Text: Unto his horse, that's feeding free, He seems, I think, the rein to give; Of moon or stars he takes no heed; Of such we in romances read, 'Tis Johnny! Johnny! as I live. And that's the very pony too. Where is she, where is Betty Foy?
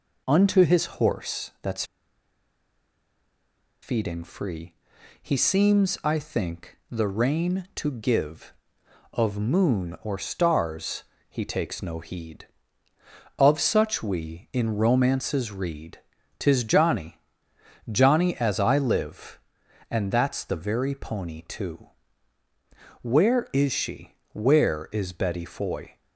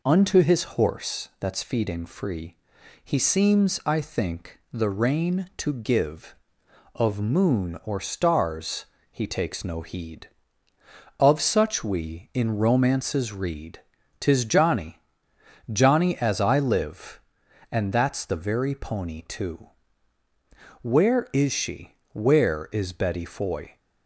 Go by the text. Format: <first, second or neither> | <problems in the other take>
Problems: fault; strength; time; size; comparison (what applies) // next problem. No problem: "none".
second | pauses between "that's" and "feeding"; strong; at 1.8 s; 1.9 s long // pauses between "stars" and "he"; slight; at 11.0 s; 0.26 s long; slight in the second